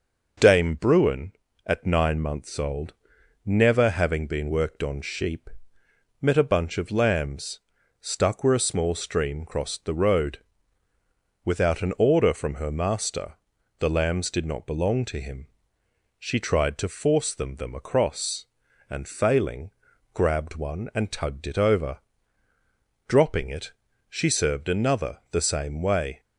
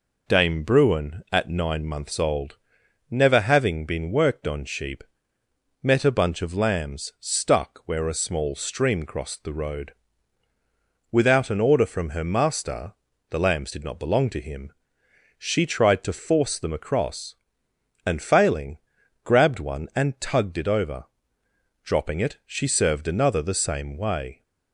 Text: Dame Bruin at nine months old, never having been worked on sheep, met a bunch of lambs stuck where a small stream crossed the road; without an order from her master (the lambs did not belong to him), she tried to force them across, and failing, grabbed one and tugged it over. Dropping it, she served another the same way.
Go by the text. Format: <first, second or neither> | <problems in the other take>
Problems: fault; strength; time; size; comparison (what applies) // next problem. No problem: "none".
second | pauses between "lambs" and "stuck"; at 7.6 s; 0.40 s long // says "them" twice; at 17.5 s